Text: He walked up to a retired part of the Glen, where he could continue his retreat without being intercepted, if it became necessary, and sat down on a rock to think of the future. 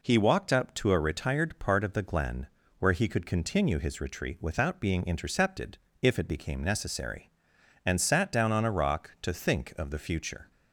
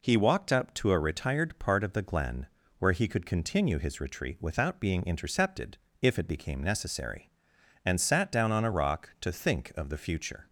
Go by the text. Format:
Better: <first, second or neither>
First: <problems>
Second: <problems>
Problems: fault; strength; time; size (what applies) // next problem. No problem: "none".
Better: neither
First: none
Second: none